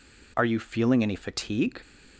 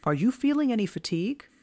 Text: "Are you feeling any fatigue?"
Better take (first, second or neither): neither